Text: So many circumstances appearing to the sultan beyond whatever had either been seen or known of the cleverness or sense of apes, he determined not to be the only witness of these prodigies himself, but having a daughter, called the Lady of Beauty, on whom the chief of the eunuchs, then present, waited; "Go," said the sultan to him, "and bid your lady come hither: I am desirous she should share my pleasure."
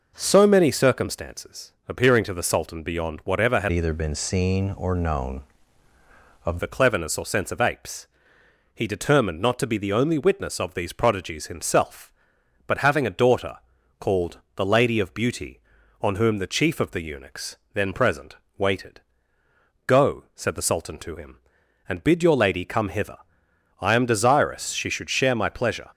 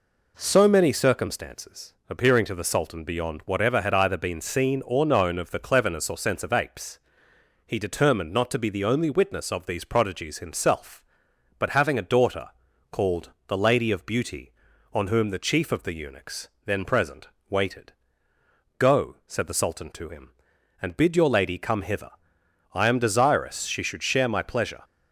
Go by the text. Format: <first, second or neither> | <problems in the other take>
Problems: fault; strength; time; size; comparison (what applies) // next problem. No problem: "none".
second | pauses between "circumstances" and "appearing"; slight; at 1.7 s; 0.18 s long; slight in the second // changes voice from "either" to "of"; from 3.7 to 6.5 s; 2.8 s long // pauses between "called" and "the"; slight; at 14.3 s; 0.16 s long; slight in the second